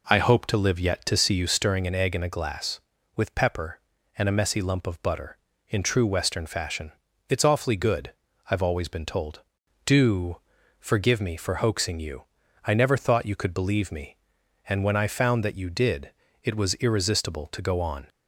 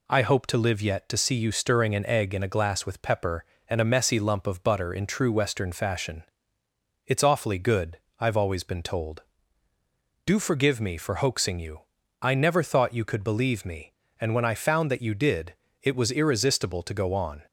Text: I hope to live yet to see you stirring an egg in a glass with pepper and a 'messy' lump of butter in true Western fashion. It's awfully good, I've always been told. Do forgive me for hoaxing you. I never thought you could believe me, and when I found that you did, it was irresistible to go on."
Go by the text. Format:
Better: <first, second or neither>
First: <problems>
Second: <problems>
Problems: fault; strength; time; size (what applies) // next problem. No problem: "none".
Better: second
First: starts louder than the rest; noticeable; until 1.7 s; 4 dB // pauses between "Do" and "forgive"; at 10.4 s; 0.38 s long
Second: none